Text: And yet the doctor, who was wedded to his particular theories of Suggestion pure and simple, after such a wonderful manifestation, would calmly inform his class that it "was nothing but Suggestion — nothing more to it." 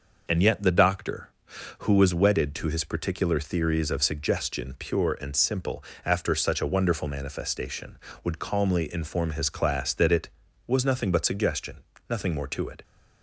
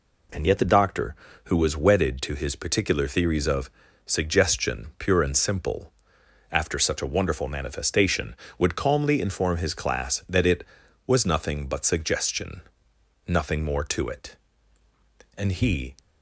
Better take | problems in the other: first | pauses between "of" and "Suggestion"; slight; at 3.7 s; 0.36 s long // goes on to say "And he"; from 15.3 s on; 0.58 s long

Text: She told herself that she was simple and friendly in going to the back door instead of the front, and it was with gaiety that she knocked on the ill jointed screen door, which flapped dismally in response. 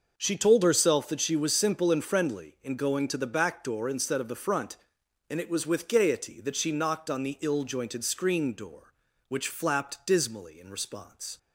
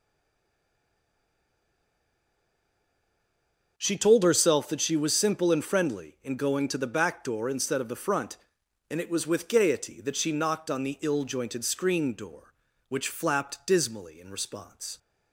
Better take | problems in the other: first | stays silent before the first word; strong; until 3.7 s; 3.7 s long

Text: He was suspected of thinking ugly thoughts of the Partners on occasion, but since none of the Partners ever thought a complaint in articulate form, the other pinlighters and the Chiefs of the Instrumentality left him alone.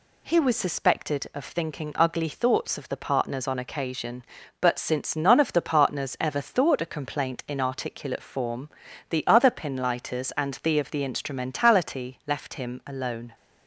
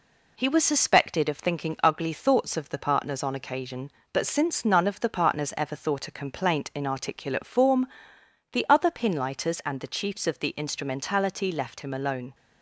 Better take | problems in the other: second | skips "Chiefs"; at 10.7 s

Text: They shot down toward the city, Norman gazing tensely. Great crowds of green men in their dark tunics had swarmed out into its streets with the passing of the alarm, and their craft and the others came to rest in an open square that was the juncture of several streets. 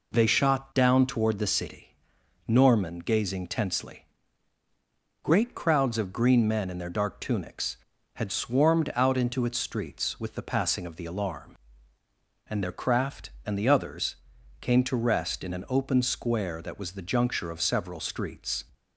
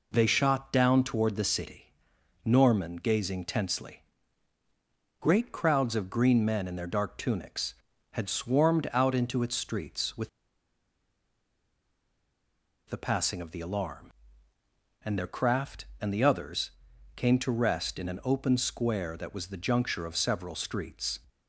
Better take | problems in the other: first | pauses between "with" and "the"; strong; at 10.2 s; 2.6 s long // pauses between "others" and "came"; noticeable; at 16.7 s; 0.46 s long; noticeable in the first

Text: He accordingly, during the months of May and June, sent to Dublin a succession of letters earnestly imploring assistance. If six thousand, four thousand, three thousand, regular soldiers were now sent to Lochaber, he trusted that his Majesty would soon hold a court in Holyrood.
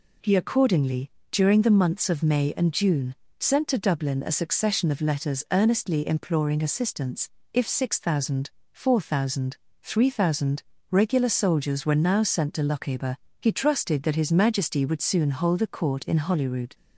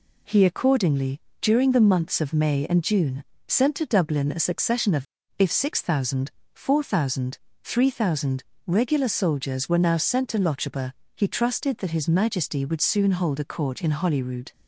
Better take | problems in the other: first | skips "letters earnestly imploring assistance"; at 5.2 s

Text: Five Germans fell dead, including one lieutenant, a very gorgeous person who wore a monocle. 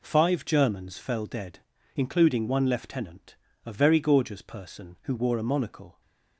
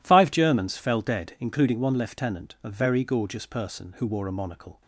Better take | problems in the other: neither | none

